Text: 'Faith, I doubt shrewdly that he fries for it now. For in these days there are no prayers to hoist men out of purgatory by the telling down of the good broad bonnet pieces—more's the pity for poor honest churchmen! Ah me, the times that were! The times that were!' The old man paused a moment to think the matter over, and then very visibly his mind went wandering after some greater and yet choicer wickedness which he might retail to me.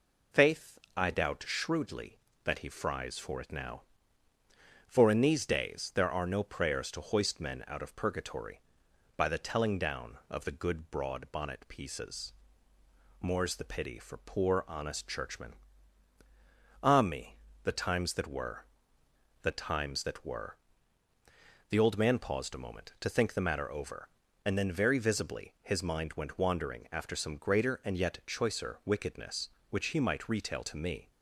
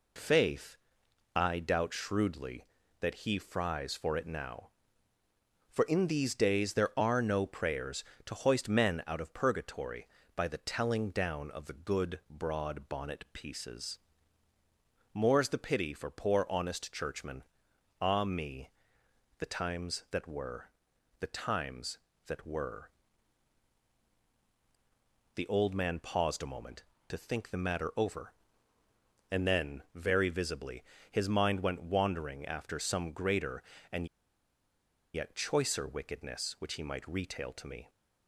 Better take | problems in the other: first | pauses between "visibly" and "his"; slight; at 30.8 s; 0.26 s long // pauses between "and" and "yet"; at 34.0 s; 1.0 s long

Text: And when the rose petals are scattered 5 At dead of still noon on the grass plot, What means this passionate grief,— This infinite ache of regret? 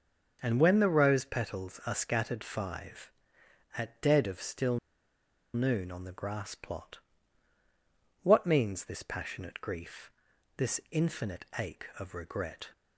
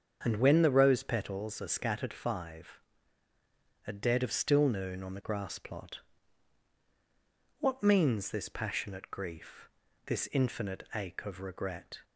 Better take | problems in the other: second | starts louder than the rest; until 1.4 s; 6.5 dB; strong in the second // pauses between "still" and "noon"; noticeable; at 4.7 s; 0.77 s long

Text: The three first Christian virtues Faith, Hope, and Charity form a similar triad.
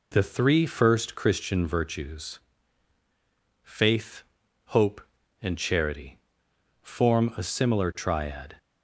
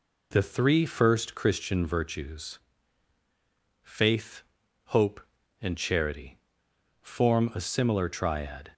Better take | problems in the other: neither | pauses between "virtues" and "Faith"; the same in both // pauses between "Charity" and "form"; noticeable; the same in both

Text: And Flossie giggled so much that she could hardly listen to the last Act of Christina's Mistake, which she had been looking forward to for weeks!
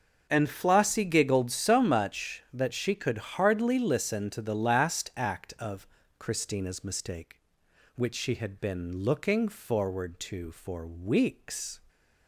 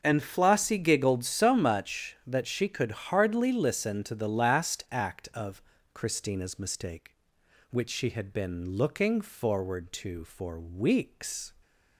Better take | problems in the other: neither | pauses between "of" and "Christina's"; slight; the same in both

